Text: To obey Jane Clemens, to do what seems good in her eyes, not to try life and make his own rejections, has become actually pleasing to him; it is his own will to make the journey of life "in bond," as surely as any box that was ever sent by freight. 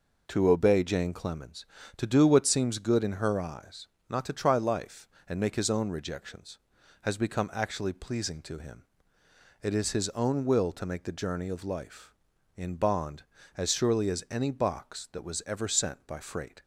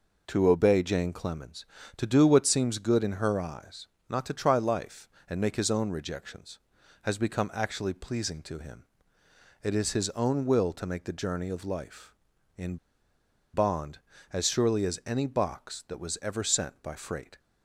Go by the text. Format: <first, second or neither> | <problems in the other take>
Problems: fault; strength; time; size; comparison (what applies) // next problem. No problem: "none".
first | pauses between "in" and "bond"; noticeable; at 12.7 s; 0.76 s long